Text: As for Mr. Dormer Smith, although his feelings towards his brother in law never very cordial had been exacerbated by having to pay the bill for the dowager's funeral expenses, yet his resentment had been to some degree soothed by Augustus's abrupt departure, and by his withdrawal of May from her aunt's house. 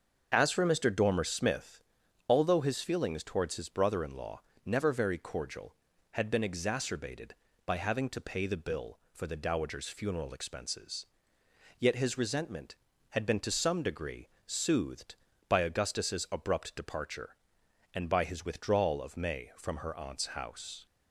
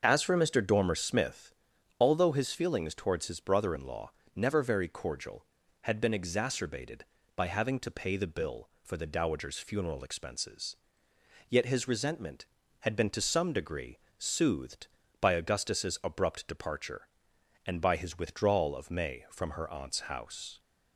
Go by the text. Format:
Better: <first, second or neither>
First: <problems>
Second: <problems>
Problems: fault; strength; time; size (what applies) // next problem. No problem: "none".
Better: neither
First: starts louder than the rest; noticeable; until 1.3 s; 6 dB // pauses between "law" and "never"; slight; at 4.4 s; 0.24 s long // pauses between "degree" and "soothed"; slight; at 14.2 s; 0.20 s long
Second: starts louder than the rest; noticeable; until 1.0 s; 6 dB // pauses between "law" and "never"; slight; at 4.1 s; 0.24 s long // pauses between "degree" and "soothed"; slight; at 13.9 s; 0.22 s long